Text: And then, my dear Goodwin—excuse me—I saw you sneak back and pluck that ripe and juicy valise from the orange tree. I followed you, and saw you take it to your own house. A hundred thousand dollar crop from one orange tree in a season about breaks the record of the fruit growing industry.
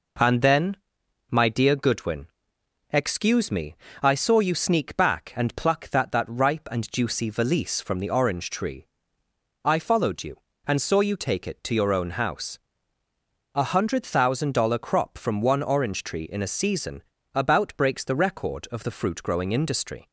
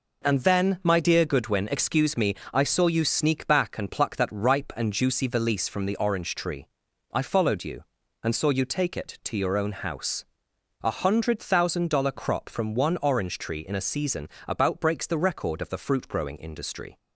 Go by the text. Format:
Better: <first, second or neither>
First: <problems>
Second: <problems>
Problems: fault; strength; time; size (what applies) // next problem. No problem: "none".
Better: second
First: says "that" twice; at 6.1 s // pauses between "season" and "about"; slight; at 17.0 s; 0.32 s long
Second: pauses between "season" and "about"; slight; at 14.2 s; 0.20 s long